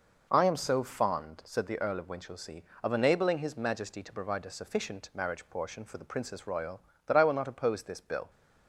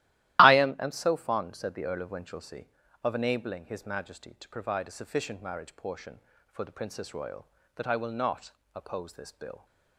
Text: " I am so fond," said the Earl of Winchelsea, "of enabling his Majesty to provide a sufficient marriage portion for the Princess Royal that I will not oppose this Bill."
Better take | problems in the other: first | starts louder than the rest; strong; until 1.4 s; 14.5 dB // says "am" twice; at 0.7 s // pauses between "not" and "oppose"; slight; at 8.5 s; 0.20 s long

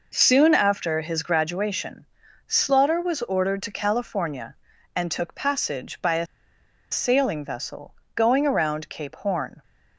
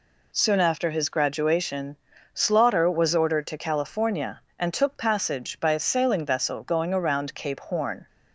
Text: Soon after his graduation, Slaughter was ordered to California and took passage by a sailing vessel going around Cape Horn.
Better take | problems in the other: second | pauses between "a" and "sailing"; noticeable; at 6.2 s; 0.66 s long // pauses between "vessel" and "going"; slight; at 7.9 s; 0.18 s long

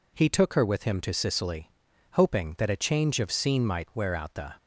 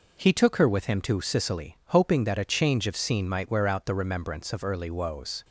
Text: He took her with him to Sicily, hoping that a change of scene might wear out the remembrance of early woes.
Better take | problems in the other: second | stops before "remembrance of early woes"; at 4.5 s

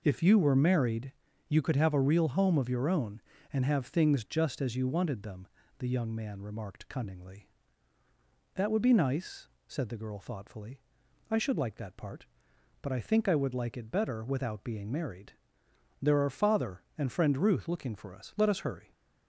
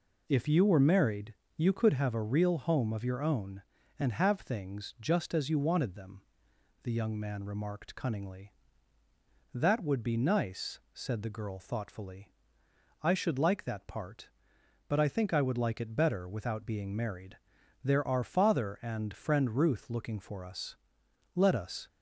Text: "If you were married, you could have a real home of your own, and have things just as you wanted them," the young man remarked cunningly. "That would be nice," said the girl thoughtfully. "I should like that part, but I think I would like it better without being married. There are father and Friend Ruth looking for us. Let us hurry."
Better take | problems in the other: first | stops before "hurry"; at 21.8 s

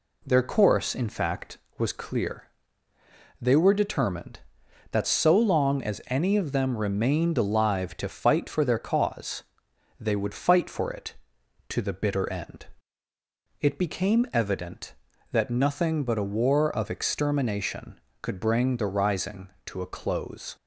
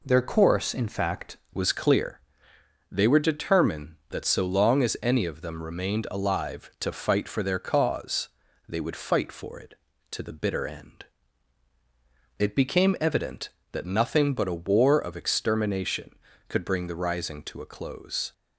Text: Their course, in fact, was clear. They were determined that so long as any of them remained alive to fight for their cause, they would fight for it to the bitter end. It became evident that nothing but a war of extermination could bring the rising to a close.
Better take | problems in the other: first | changes voice at "was"; from 1.5 s on; 16.8 s long

